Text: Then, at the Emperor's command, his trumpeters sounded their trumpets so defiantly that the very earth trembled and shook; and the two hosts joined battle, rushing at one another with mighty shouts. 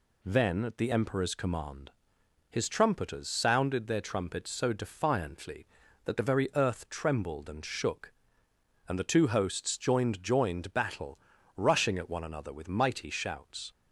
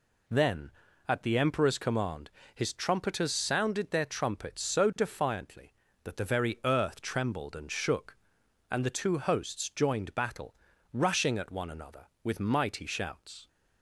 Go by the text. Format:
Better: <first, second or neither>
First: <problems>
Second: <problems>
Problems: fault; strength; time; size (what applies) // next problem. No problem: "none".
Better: second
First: says "joined" twice; at 10.2 s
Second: none